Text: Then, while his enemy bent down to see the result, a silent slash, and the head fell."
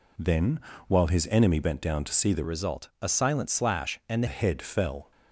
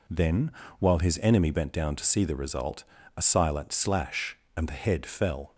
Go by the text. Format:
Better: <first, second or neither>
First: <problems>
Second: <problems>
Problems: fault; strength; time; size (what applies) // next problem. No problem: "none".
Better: second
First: changes voice from "result" to "the"; from 2.4 to 4.2 s; 1.8 s long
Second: none